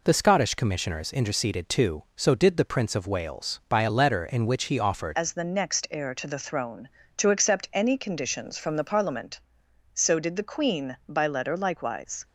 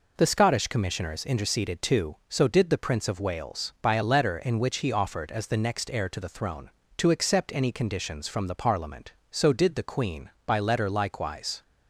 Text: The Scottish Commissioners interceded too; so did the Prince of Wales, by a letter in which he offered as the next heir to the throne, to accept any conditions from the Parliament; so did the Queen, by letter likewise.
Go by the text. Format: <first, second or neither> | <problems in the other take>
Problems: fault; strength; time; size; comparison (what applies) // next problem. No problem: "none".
second | changes voice at "as"; from 5.1 s on; 7.1 s long